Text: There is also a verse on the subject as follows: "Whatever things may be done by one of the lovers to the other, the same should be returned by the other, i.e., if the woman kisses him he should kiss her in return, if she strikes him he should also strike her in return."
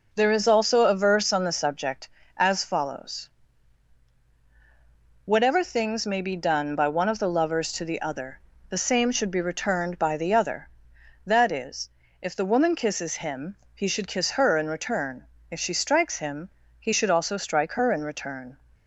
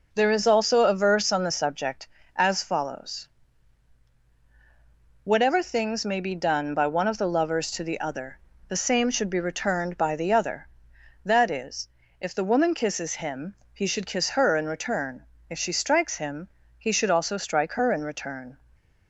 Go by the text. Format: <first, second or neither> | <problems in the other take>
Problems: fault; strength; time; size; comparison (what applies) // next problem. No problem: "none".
neither | pauses between "him" and "he"; slight; the same in both // pauses between "him" and "he"; slight; the same in both